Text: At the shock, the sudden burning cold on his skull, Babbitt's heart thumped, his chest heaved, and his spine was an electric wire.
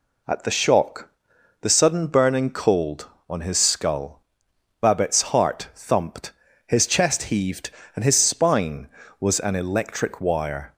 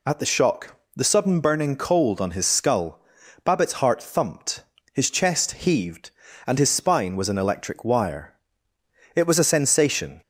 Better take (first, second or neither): first